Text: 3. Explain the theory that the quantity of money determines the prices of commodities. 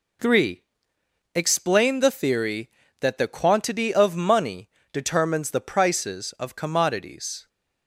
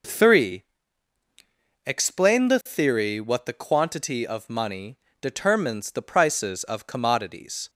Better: first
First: pauses between "money" and "determines"; slight; at 4.6 s; 0.24 s long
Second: says "what" for "that"; at 3.1 s // pauses between "money" and "determines"; slight; at 4.9 s; 0.24 s long

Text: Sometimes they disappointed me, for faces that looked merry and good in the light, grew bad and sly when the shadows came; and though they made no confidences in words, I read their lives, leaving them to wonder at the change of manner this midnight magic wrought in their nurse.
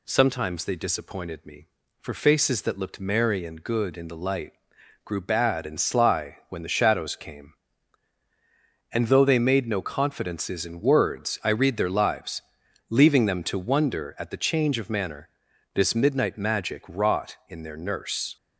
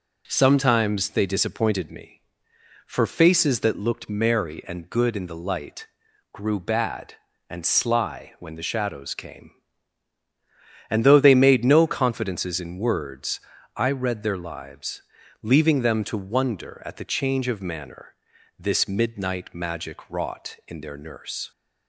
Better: neither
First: pauses between "manner" and "this"; noticeable; at 15.2 s; 0.46 s long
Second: pauses between "manner" and "this"; at 18.1 s; 0.42 s long

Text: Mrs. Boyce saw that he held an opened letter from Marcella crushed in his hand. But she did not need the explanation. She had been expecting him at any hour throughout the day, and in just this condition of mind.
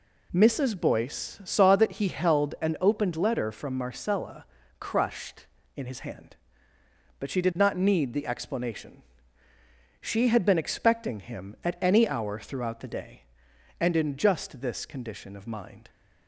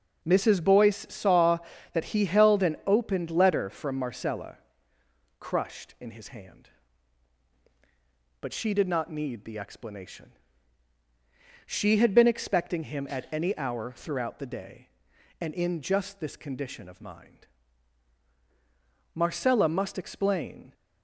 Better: first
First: pauses between "Marcella" and "crushed"; slight; at 4.4 s; 0.34 s long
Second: pauses between "Marcella" and "crushed"; noticeable; at 4.5 s; 0.82 s long // goes on to say "Marcella must explain"; from 19.1 s on; 1.5 s long

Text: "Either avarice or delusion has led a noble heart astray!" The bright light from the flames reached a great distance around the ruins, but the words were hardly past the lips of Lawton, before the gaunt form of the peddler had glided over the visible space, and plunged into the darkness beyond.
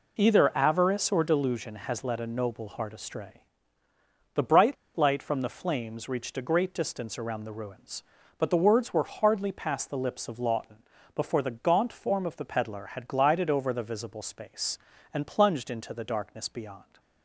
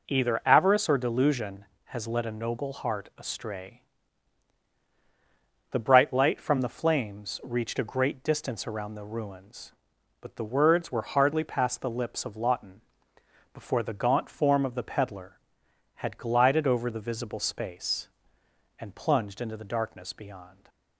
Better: second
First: pauses between "bright" and "light"; slight; at 4.7 s; 0.21 s long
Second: none

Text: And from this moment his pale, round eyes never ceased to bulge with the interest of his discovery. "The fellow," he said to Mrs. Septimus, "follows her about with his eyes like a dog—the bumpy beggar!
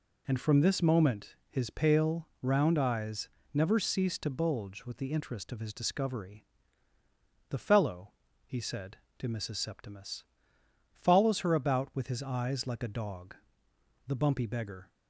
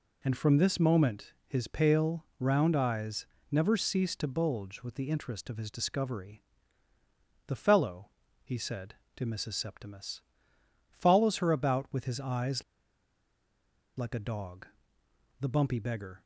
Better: first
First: pauses between "eyes" and "never"; slight; at 3.2 s; 0.26 s long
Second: pauses between "eyes" and "never"; slight; at 3.2 s; 0.26 s long // pauses between "eyes" and "like"; strong; at 12.6 s; 1.3 s long

